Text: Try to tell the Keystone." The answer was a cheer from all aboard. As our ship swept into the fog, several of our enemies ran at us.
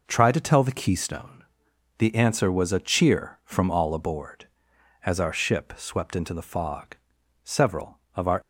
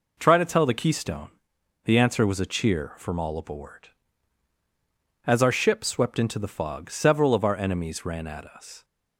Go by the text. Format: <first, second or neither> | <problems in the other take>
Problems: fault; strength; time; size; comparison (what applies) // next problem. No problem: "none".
second | stops before "enemies ran at us"; at 8.4 s